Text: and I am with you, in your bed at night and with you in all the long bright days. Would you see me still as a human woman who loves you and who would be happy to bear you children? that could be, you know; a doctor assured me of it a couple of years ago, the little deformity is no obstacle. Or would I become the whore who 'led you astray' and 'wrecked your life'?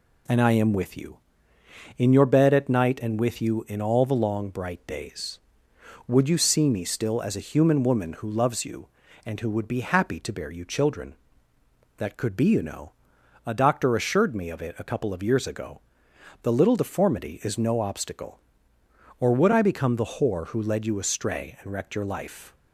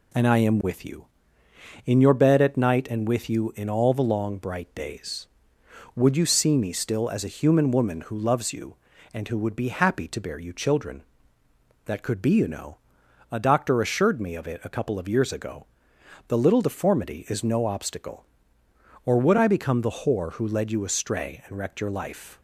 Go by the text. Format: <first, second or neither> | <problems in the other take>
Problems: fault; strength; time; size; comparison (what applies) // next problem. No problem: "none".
neither | none